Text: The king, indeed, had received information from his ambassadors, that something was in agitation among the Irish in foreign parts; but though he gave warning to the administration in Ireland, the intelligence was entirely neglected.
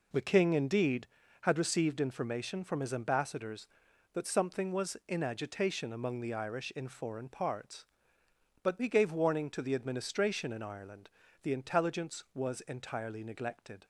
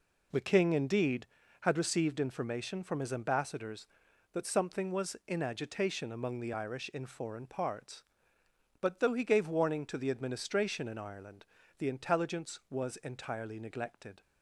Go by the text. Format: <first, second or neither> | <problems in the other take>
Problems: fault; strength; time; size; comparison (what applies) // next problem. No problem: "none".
second | skips "though"; at 8.8 s